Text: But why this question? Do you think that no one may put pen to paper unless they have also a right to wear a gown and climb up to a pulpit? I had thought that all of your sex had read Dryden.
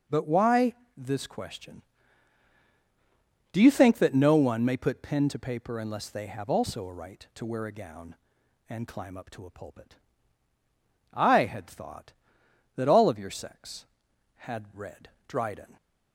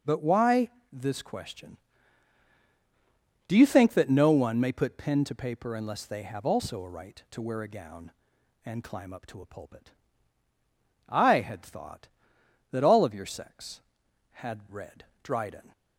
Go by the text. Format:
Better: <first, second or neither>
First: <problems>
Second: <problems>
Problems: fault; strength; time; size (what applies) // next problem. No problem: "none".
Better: neither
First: pauses between "why" and "this"; slight; at 0.7 s; 0.24 s long // pauses between "read" and "Dryden"; slight; at 15.0 s; 0.20 s long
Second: pauses between "why" and "this"; slight; at 0.6 s; 0.24 s long // pauses between "read" and "Dryden"; slight; at 15.0 s; 0.20 s long